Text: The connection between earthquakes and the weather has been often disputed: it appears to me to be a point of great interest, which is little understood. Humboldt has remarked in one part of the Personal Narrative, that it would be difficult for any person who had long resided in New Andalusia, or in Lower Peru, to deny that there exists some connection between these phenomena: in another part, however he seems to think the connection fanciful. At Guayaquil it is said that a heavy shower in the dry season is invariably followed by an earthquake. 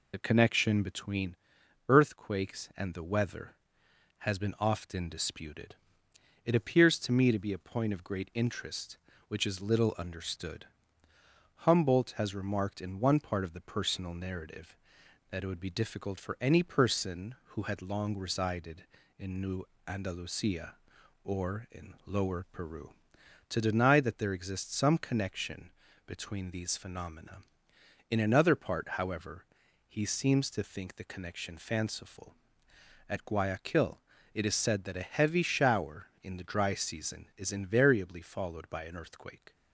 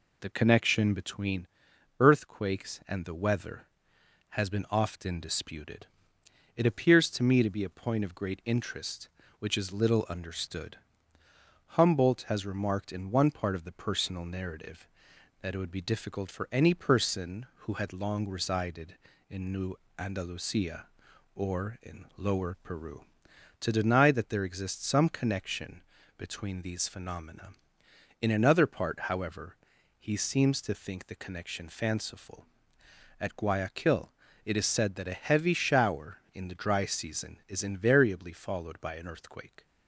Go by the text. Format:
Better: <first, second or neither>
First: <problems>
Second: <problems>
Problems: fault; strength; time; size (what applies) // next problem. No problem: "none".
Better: second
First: loses the start of "The"; at 0.1 s; 30 ms // pauses between "between" and "earthquakes"; noticeable; at 1.3 s; 0.50 s long // pauses between "New" and "Andalusia"; slight; at 19.6 s; 0.22 s long // pauses between "connection" and "between"; at 25.6 s; 0.38 s long // pauses between "however" and "he"; noticeable; at 29.4 s; 0.46 s long // pauses between "Guayaquil" and "it"; slight; at 33.9 s; 0.36 s long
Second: pauses between "between" and "earthquakes"; noticeable; at 1.4 s; 0.50 s long // pauses between "New" and "Andalusia"; slight; at 19.7 s; 0.22 s long // pauses between "connection" and "between"; at 25.7 s; 0.38 s long // pauses between "however" and "he"; noticeable; at 29.5 s; 0.46 s long // pauses between "Guayaquil" and "it"; slight; at 34.0 s; 0.36 s long